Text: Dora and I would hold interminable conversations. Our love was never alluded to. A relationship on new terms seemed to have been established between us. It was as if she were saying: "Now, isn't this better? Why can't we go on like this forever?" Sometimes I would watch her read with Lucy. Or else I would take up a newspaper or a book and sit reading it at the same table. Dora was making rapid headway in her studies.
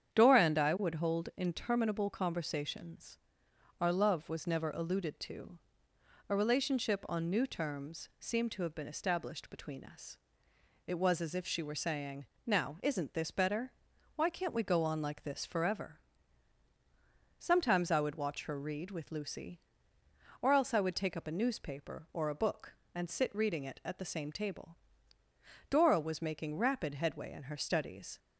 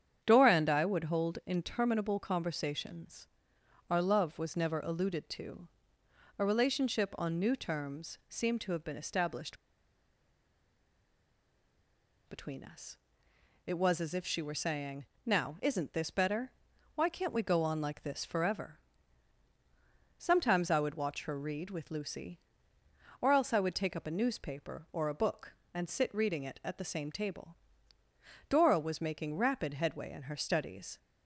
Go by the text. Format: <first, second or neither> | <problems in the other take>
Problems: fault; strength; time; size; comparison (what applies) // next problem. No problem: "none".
first | starts louder than the rest; strong; until 1.2 s; 8.5 dB; strong in the first // pauses between "established" and "between"; strong; at 9.5 s; 2.7 s long